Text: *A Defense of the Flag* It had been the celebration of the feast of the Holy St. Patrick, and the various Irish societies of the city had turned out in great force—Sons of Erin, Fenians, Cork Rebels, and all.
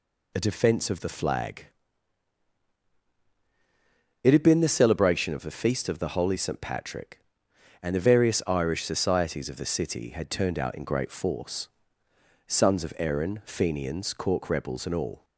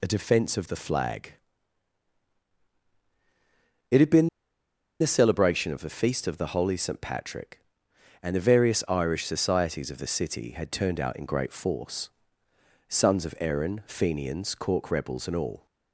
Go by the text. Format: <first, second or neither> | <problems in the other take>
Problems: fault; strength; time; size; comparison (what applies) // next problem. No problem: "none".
first | pauses between "Flag" and "It"; strong; at 1.3 s; 2.5 s long; strong in the first // pauses between "been" and "the"; noticeable; at 4.2 s; 0.72 s long